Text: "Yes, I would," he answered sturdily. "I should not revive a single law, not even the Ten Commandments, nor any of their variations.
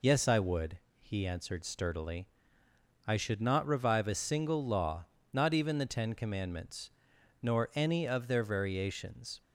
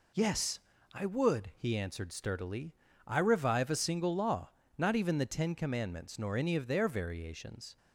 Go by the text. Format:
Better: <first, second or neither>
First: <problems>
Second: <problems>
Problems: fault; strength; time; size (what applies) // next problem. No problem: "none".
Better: first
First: none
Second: skips "should not"; at 3.1 s